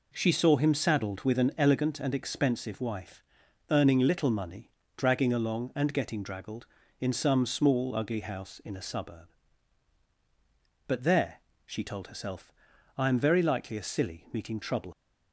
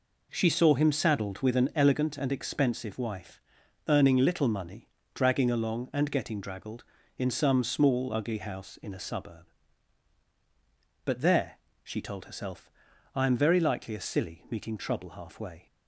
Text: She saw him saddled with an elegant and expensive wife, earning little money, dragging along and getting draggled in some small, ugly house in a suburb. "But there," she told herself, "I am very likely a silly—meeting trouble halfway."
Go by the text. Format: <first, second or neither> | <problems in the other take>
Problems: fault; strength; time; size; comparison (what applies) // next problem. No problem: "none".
second | stops before "halfway"; at 14.9 s